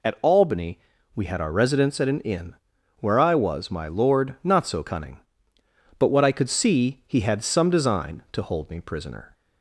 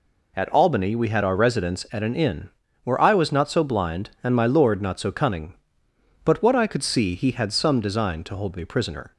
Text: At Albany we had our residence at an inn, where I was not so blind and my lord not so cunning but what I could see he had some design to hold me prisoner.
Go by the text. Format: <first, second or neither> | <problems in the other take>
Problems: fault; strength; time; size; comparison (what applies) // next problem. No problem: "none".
second | pauses between "Albany" and "we"; slight; at 0.7 s; 0.36 s long // skips "not so blind and"; at 3.7 s